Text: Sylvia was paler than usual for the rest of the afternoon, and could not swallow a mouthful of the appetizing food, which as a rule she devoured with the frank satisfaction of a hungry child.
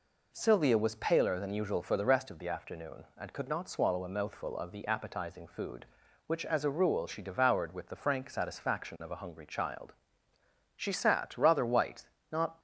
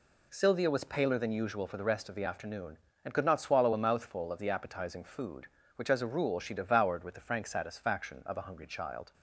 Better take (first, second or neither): second